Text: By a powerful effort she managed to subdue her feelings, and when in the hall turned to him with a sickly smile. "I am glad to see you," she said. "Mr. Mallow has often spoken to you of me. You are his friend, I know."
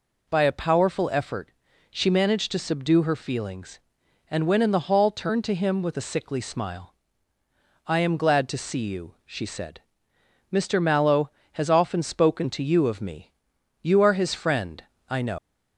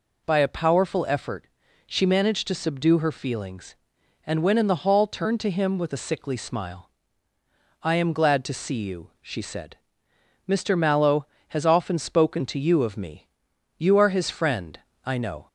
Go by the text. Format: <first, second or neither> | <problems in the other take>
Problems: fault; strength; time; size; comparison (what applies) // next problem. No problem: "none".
second | pauses between "effort" and "she"; at 1.5 s; 0.40 s long; also in the second // leaves "know" unfinished; at 15.3 s; 130 ms